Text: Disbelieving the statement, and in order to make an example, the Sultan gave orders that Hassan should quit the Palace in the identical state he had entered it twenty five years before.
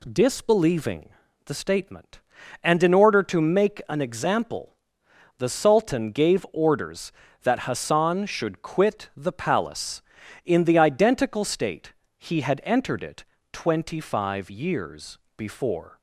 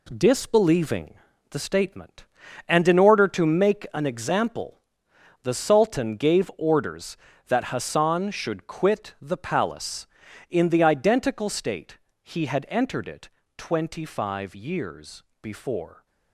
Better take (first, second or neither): first